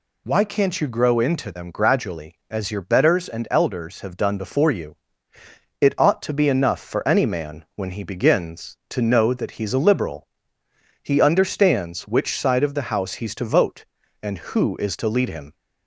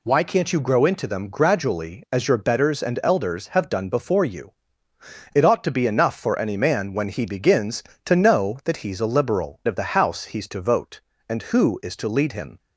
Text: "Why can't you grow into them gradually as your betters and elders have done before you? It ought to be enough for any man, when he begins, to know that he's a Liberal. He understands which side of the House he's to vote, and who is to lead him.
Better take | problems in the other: first | skips "He understands which side"; at 9.6 s

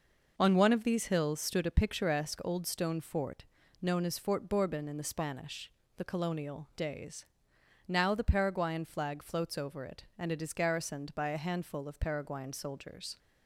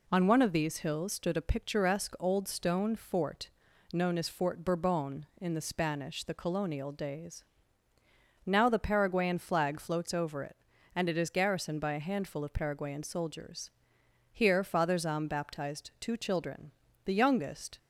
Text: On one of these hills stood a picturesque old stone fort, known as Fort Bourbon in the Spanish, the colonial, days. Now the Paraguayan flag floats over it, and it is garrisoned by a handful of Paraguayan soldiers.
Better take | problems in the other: first | goes on to say "Here Father Zahm baptized two children the youngest"; strong; from 14.3 s on; 3.4 s long

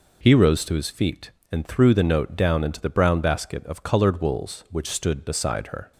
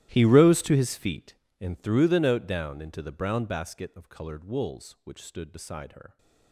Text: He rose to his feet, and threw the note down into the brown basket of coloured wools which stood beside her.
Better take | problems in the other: first | gets quieter; strong; throughout; 20.5 dB

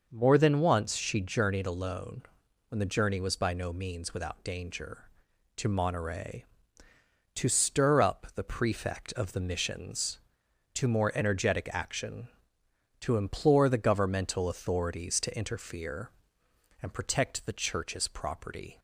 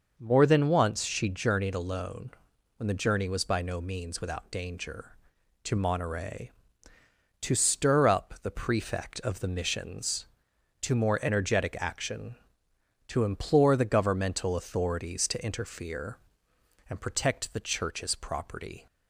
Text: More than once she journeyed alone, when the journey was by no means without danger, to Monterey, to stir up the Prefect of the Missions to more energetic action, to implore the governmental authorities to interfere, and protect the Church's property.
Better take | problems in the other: neither | none

